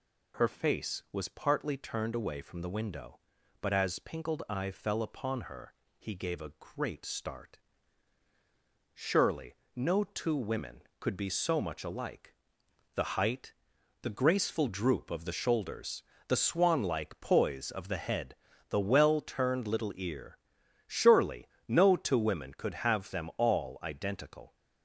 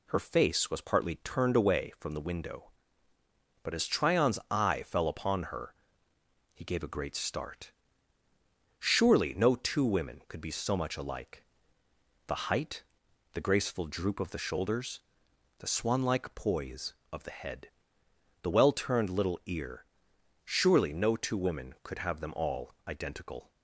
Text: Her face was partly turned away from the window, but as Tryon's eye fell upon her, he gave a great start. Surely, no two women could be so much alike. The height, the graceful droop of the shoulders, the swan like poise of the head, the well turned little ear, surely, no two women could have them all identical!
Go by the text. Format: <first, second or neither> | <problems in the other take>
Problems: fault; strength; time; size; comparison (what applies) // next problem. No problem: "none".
second | says "Pinkled" for "Tryon's"; at 3.9 s